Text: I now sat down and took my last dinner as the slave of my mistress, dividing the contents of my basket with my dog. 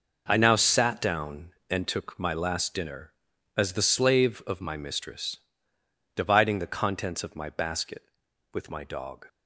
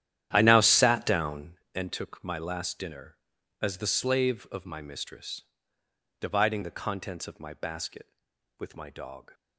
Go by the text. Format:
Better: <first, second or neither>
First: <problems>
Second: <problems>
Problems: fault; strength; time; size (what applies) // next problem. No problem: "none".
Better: first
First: none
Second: starts louder than the rest; strong; until 1.6 s; 11 dB